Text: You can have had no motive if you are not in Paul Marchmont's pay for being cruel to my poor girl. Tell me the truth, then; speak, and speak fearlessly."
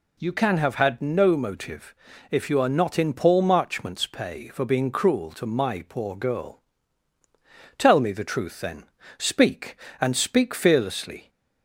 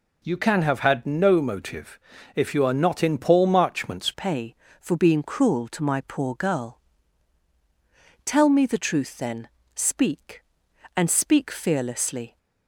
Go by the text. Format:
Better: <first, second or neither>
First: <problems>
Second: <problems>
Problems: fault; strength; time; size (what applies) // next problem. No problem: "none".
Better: first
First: pauses between "motive" and "if"; slight; at 1.9 s; 0.36 s long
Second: pauses between "motive" and "if"; slight; at 1.9 s; 0.36 s long // changes voice at "pay"; from 4.1 s on; 8.2 s long